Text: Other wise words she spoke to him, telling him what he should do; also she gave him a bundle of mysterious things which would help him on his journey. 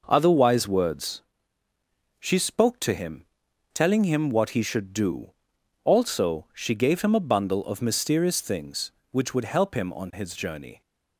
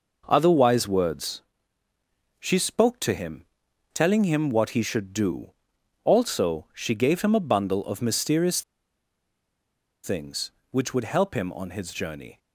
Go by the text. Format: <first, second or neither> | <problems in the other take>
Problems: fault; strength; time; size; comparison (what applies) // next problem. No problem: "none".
first | pauses between "words" and "she"; noticeable; at 1.4 s; 0.98 s long; noticeable in the first // pauses between "mysterious" and "things"; strong; at 8.6 s; 1.4 s long